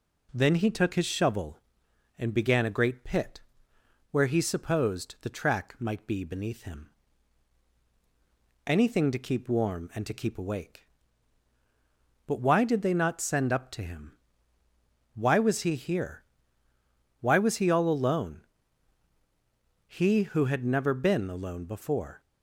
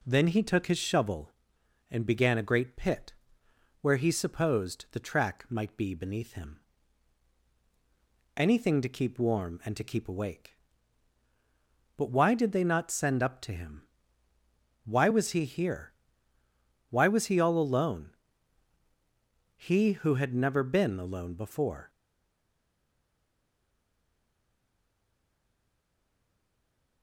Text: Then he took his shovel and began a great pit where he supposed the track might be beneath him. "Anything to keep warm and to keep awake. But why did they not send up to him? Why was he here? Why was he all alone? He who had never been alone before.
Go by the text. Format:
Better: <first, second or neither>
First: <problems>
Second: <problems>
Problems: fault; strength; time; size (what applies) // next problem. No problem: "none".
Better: first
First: pauses between "pit" and "where"; noticeable; at 3.3 s; 0.72 s long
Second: pauses between "pit" and "where"; noticeable; at 3.1 s; 0.70 s long // stays silent after the last word; strong; from 21.8 s on; 5.2 s long